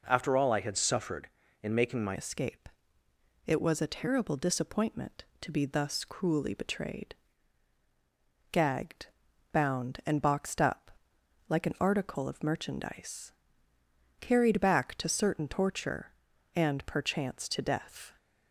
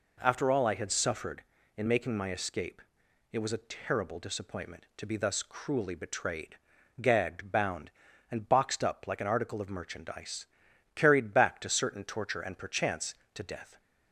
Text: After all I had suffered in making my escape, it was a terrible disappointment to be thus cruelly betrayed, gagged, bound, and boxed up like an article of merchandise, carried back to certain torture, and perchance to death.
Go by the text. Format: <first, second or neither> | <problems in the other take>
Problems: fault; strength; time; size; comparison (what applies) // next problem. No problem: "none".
second | changes voice at "escape"; from 2.1 s on; 16.0 s long // pauses between "up" and "like"; noticeable; at 10.9 s; 0.58 s long